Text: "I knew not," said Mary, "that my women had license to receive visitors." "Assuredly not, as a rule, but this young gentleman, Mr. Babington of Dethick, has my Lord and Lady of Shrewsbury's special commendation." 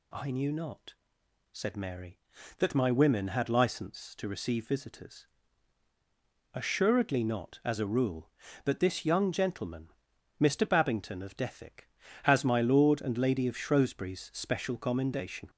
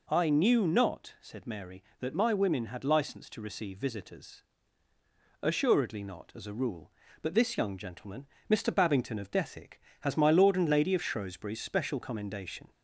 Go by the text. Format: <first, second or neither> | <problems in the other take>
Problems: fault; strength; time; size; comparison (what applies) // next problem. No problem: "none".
neither | none